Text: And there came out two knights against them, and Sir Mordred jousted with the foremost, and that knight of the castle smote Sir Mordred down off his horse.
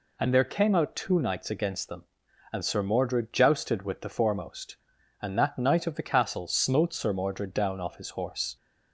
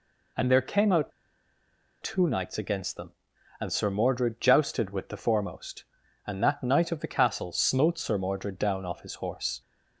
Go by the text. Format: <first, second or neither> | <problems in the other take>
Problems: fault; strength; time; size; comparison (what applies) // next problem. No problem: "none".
first | pauses between "out" and "two"; noticeable; at 1.1 s; 0.91 s long